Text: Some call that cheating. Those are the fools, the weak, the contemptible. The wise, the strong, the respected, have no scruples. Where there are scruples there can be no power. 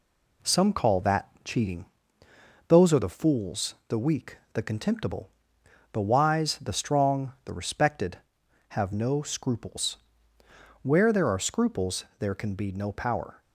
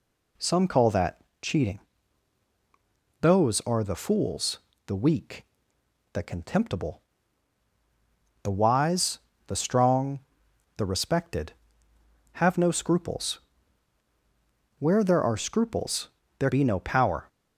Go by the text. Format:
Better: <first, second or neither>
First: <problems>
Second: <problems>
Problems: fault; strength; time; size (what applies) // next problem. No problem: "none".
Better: first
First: pauses between "that" and "cheating"; slight; at 1.2 s; 0.16 s long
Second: pauses between "that" and "cheating"; slight; at 1.1 s; 0.22 s long // pauses between "scruples" and "there"; slight; at 16.0 s; 0.30 s long // skips "can"; at 16.4 s